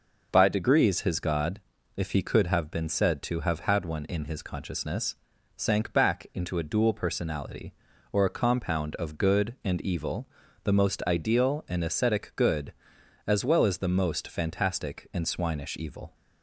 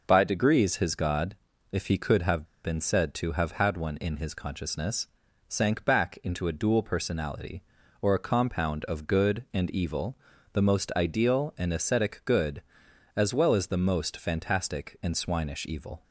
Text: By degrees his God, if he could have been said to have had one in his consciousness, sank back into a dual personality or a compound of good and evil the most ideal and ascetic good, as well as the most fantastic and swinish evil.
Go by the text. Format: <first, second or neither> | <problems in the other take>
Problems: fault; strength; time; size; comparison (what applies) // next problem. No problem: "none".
first | pauses between "have" and "been"; slight; at 2.4 s; 0.18 s long // pauses between "evil" and "the"; slight; at 10.1 s; 0.36 s long; slight in the first